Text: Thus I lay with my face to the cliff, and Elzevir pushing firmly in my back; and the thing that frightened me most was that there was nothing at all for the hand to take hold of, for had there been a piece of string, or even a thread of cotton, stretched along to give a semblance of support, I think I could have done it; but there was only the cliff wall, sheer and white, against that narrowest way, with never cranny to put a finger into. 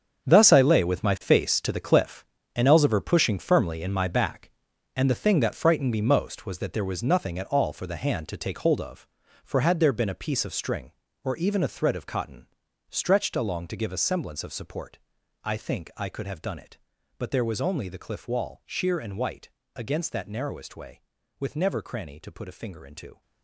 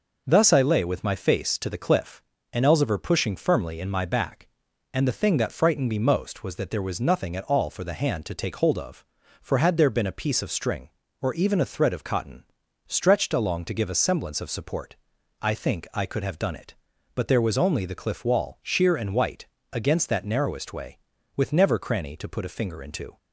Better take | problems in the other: second | gets quieter; strong; throughout; 12.5 dB

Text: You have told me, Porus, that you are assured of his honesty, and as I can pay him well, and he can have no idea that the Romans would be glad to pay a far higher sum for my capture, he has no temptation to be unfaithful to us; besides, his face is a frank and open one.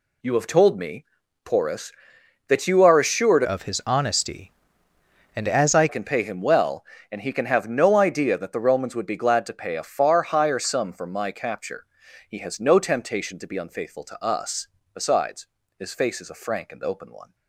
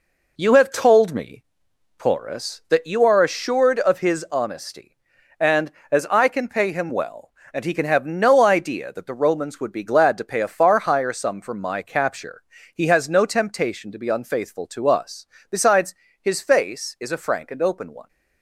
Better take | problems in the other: second | changes voice from "of" to "I"; from 3.4 to 5.8 s; 2.4 s long

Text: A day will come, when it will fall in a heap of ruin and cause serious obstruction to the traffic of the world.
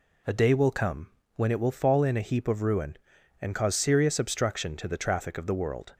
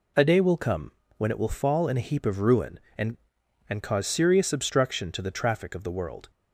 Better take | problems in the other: first | says "and" twice; at 3.6 s

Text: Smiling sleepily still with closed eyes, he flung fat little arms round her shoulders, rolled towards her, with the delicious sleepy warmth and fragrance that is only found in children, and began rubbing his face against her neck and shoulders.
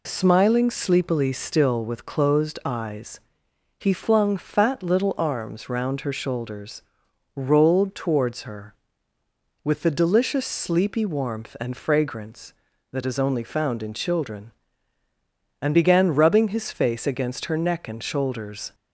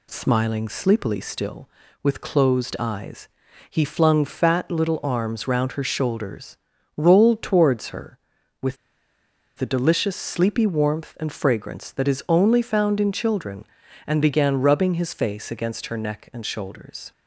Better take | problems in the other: first | pauses between "with" and "the"; noticeable; at 8.7 s; 0.82 s long

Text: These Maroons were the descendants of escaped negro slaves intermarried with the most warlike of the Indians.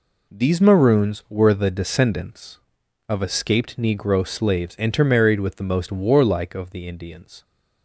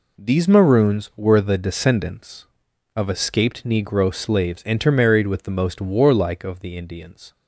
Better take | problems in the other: neither | none

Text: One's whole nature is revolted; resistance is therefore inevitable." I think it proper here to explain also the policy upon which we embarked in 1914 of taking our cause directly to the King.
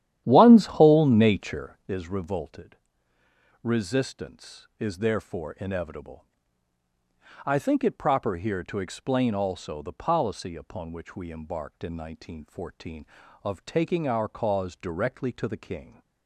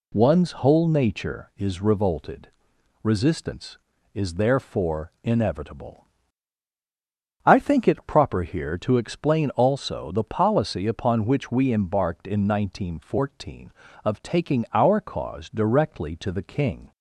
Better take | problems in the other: second | starts louder than the rest; strong; until 1.9 s; 11 dB

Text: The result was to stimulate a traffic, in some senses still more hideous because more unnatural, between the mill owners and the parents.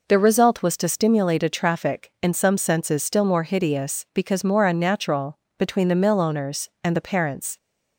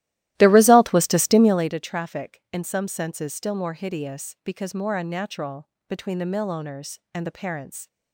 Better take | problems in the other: first | starts louder than the rest; strong; until 1.8 s; 15 dB

